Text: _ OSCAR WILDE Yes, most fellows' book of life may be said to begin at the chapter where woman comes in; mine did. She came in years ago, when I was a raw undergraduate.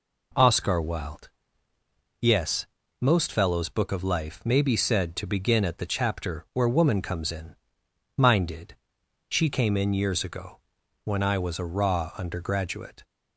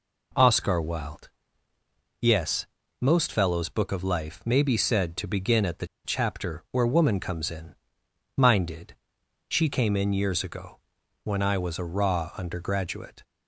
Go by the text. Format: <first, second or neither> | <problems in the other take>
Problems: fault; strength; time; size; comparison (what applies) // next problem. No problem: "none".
first | pauses between "WILDE" and "Yes"; noticeable; at 1.2 s; 0.90 s long; noticeable in the first // pauses between "the" and "chapter"; slight; at 5.8 s; 0.20 s long